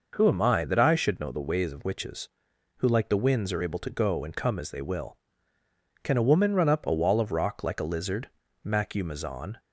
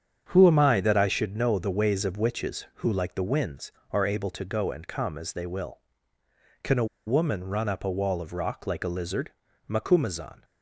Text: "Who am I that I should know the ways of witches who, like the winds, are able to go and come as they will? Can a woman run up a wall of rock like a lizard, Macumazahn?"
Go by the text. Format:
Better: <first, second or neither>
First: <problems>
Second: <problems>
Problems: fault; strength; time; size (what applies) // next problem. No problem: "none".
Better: first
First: none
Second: starts louder than the rest; strong; until 1.3 s; 7.5 dB // pauses between "a" and "woman"; slight; at 6.8 s; 0.21 s long